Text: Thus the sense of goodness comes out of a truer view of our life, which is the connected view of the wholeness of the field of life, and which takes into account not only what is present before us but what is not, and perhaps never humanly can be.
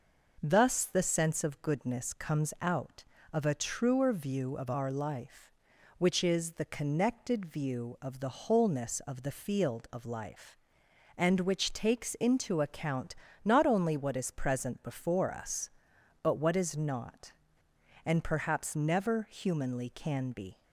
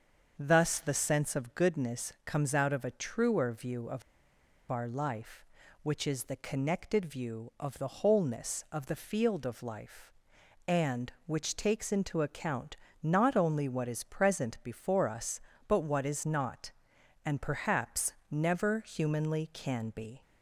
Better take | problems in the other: first | starts louder than the rest; until 1.3 s; 6.5 dB // pauses between "of" and "our"; noticeable; at 4.0 s; 0.68 s long // pauses between "account" and "not"; slight; at 12.7 s; 0.24 s long; slight in the first // pauses between "perhaps" and "never"; slight; at 18.1 s; 0.16 s long

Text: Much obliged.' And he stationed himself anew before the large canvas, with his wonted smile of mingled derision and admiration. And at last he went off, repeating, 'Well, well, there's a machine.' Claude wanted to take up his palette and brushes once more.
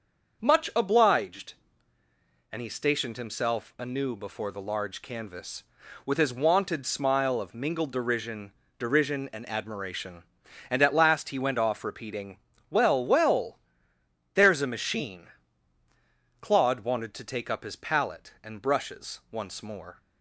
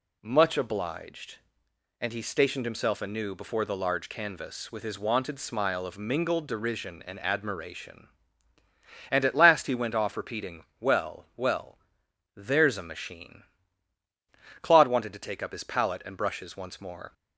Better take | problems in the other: second | starts louder than the rest; until 1.4 s; 6.5 dB // says "derision" twice; at 8.7 s

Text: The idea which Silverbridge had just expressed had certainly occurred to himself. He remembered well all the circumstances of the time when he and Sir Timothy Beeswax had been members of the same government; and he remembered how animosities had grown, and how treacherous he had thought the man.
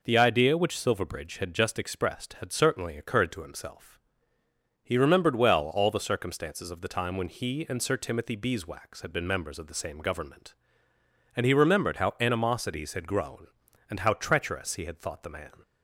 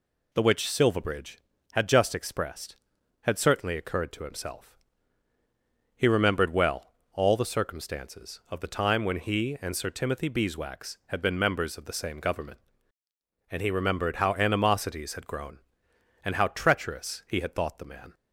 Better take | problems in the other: first | skips "idea"; at 0.4 s // pauses between "well" and "all"; slight; at 6.9 s; 0.18 s long

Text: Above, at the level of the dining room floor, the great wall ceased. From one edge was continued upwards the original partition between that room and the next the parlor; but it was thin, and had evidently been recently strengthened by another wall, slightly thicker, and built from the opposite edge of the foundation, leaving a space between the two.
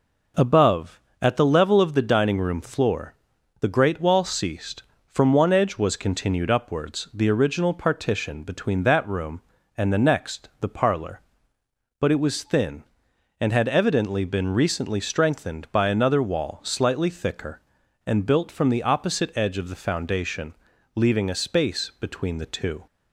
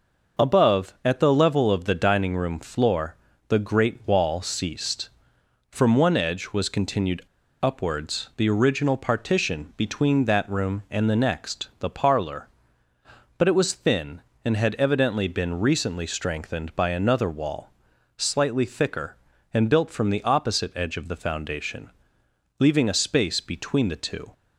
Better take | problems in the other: first | pauses between "continued" and "upwards"; at 7.2 s; 0.40 s long

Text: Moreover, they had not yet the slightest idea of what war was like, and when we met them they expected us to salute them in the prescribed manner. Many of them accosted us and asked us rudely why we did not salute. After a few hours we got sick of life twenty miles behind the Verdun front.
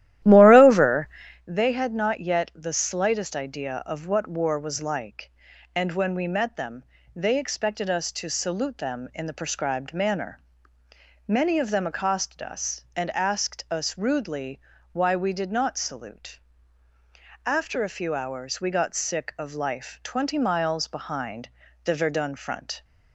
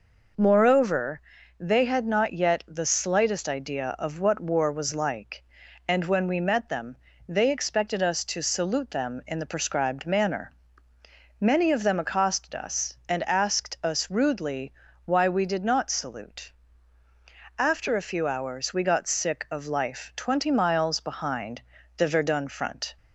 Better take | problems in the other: second | starts louder than the rest; strong; until 1.5 s; 13.5 dB // pauses between "them" and "they"; slight; at 6.8 s; 0.32 s long; slight in the second // pauses between "rudely" and "why"; slight; at 14.6 s; 0.32 s long; slight in the second // pauses between "behind" and "the"; slight; at 21.4 s; 0.34 s long; slight in the second

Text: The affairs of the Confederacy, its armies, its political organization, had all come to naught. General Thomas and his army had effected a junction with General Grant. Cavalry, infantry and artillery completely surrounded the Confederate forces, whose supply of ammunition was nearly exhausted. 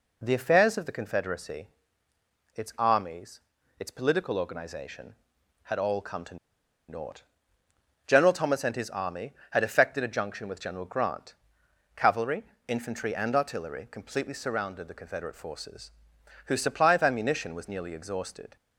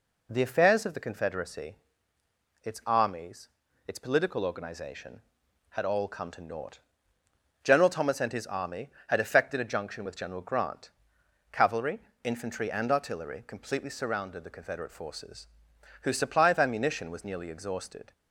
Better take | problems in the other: second | pauses between "to" and "naught"; noticeable; at 6.3 s; 0.52 s long

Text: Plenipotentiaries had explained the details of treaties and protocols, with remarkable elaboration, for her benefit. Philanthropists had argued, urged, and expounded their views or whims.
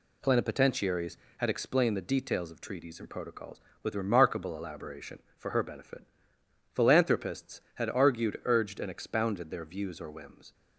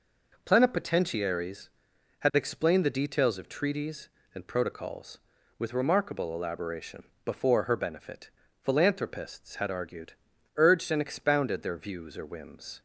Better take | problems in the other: first | says "before" for "for"; at 7.2 s

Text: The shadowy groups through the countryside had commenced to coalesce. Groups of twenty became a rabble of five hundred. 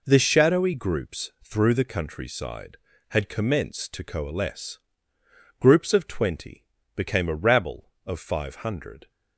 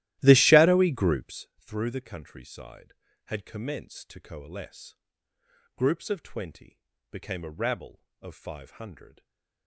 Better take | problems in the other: first | starts louder than the rest; strong; until 1.4 s; 15 dB // pauses between "twenty" and "became"; slight; at 6.7 s; 0.32 s long; slight in the first // stays silent after the last word; slight; from 9.0 s on; 0.6 s long

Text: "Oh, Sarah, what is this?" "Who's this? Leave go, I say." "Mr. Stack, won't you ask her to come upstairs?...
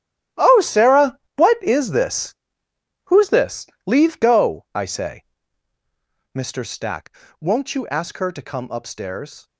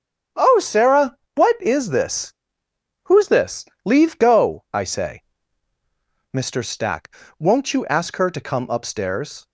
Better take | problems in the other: second | gets quieter; strong; throughout; 15.5 dB // starts louder than the rest; strong; until 1.5 s; 13 dB; strong in the second

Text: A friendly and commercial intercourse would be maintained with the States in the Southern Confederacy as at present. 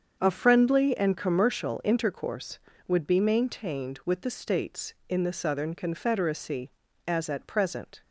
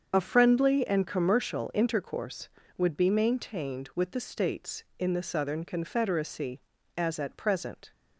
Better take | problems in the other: first | loses the start of "A"; at 0.1 s; 35 ms // starts louder than the rest; until 1.1 s; 7 dB; strong in the first

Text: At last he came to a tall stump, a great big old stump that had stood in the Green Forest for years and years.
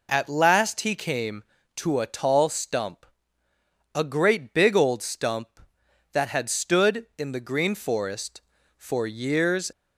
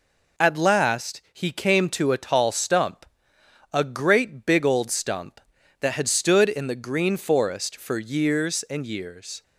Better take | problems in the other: second | stops before "and years"; at 9.7 s

